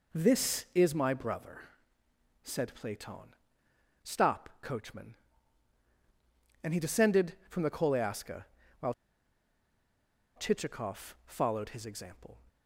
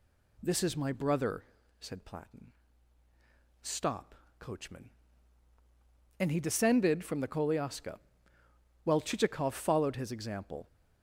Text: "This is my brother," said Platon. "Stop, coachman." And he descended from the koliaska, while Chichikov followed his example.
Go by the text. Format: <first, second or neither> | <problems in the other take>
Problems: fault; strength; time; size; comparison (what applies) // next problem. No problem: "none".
second | pauses between "while" and "Chichikov"; strong; at 8.9 s; 1.4 s long